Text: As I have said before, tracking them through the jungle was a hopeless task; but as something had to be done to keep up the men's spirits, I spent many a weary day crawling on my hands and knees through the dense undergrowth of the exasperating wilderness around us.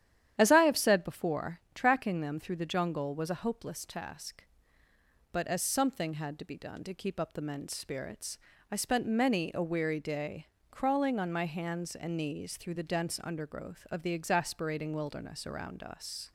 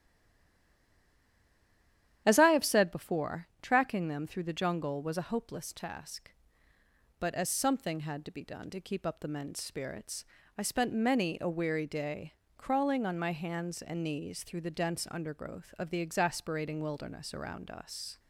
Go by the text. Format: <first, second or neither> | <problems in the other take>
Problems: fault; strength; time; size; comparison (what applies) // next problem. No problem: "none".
first | stays silent before the first word; until 2.2 s; 2.2 s long // starts louder than the rest; strong; until 3.2 s; 10.5 dB; strong in the first // pauses between "day" and "crawling"; slight; at 12.3 s; 0.24 s long; slight in the first